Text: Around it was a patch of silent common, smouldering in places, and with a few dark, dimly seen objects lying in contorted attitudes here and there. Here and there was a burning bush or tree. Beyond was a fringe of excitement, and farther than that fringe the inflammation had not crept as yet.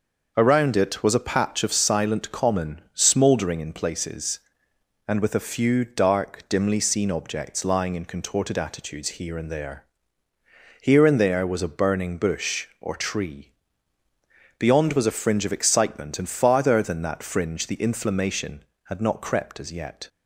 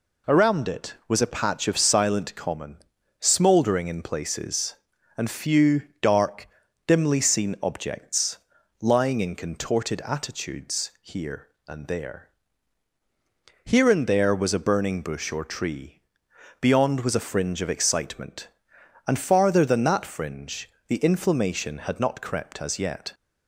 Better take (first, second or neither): first